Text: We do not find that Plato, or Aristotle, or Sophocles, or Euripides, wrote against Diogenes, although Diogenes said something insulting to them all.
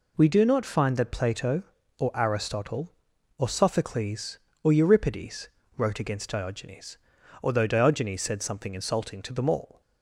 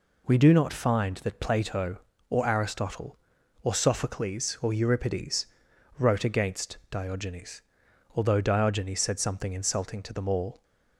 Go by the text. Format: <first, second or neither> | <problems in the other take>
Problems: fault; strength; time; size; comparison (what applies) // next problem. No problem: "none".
neither | none